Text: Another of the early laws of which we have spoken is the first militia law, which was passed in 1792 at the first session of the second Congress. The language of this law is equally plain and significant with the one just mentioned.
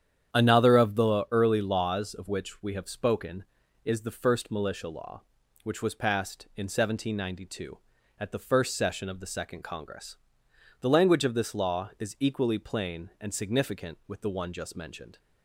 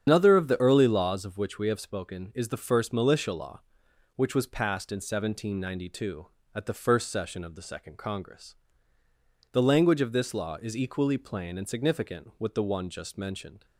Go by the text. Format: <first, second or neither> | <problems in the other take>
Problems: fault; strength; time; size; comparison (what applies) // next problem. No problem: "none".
first | loses the start of "Another"; at 0.0 s; 120 ms // starts louder than the rest; strong; until 1.0 s; 8.5 dB; strong in the first